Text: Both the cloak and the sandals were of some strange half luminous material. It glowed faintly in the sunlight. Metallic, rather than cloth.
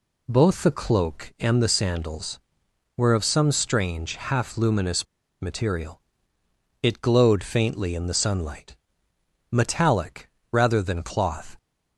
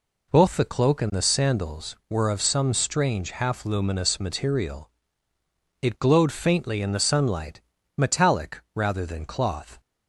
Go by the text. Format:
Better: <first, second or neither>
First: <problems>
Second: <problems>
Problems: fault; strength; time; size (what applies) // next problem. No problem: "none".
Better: second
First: pauses between "luminous" and "material"; slight; at 5.0 s; 0.35 s long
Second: none